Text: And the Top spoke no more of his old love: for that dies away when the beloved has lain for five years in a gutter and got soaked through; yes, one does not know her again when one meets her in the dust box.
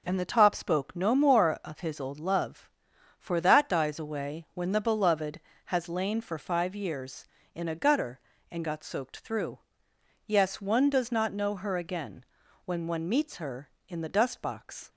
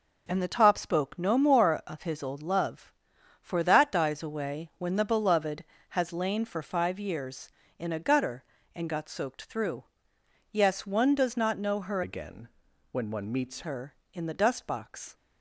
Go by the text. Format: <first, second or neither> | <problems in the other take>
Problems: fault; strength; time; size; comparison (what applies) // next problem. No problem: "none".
first | changes voice from "again" to "meets"; from 12.0 to 13.6 s; 1.6 s long // pauses between "again" and "when"; noticeable; at 12.4 s; 0.46 s long; also in the first